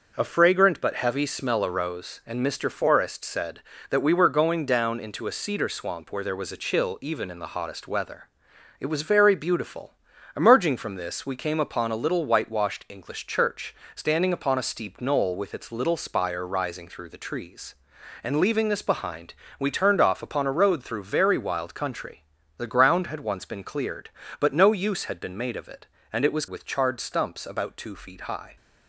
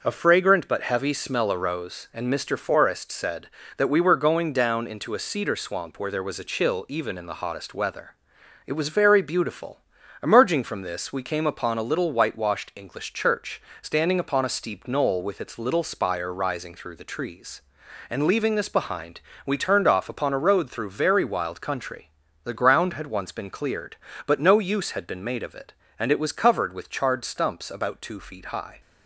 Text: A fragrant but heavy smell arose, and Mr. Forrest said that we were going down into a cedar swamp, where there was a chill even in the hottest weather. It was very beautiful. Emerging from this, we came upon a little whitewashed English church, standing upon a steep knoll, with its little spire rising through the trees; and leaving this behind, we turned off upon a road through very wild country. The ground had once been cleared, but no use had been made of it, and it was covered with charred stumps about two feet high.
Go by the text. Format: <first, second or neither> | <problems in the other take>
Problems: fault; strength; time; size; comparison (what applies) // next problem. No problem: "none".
second | starts louder than the rest; noticeable; until 1.1 s; 6 dB; noticeable in the second // skips "covered"; at 26.4 s